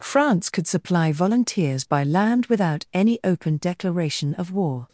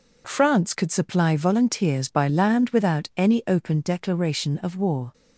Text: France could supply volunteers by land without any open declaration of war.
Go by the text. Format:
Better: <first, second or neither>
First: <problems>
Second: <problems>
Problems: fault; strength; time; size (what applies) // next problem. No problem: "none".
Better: neither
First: none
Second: none